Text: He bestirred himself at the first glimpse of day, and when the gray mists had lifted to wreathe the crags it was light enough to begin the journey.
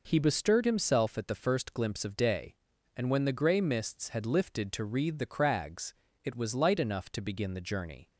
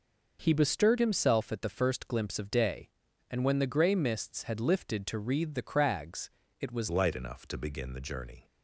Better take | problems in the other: first | pauses between "crags" and "it"; slight; at 6.3 s; 0.30 s long; slight in the first // changes voice at "light"; from 6.8 s on; 1.6 s long

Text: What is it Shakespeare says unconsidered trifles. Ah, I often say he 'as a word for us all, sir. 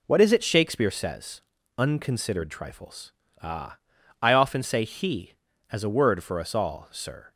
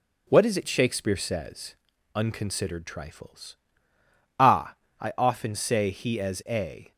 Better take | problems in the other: first | pauses between "says" and "unconsidered"; at 1.7 s; 0.38 s long; also in the first // stops before "word for us all sir"; at 6.9 s

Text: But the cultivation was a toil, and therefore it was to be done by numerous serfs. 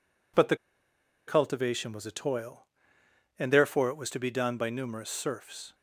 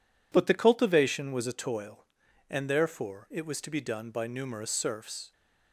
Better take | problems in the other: second | pauses between "the" and "cultivation"; noticeable; at 0.5 s; 0.70 s long

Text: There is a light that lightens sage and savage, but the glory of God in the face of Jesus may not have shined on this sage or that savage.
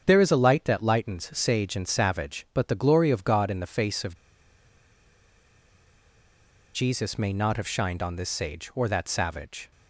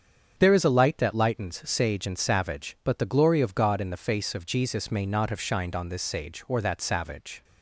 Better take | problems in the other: second | starts louder than the rest; strong; until 1.0 s; 7.5 dB; strong in the second // pauses between "of" and "Jesus"; strong; at 4.1 s; 2.5 s long

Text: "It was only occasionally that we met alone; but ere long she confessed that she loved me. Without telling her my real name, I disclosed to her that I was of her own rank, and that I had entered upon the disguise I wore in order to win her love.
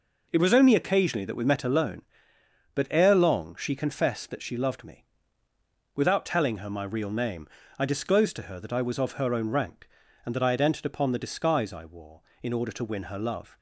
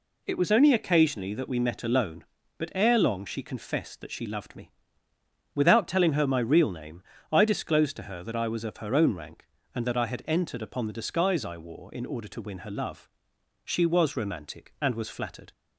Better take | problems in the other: first | goes on to say "She was romantic and was flattered"; strong; from 13.6 s on; 1.8 s long

